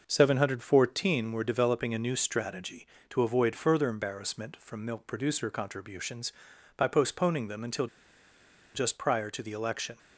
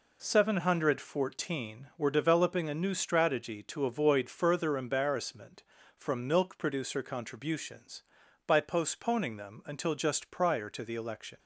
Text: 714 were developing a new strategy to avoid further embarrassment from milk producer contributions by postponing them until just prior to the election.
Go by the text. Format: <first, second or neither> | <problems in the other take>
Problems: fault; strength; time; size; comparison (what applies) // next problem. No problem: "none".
second | pauses between "until" and "just"; noticeable; at 7.8 s; 0.88 s long